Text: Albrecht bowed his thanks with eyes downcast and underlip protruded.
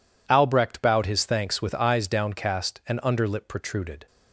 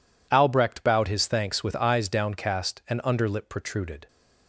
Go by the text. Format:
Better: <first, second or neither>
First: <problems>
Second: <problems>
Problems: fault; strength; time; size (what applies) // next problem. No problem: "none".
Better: neither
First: none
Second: none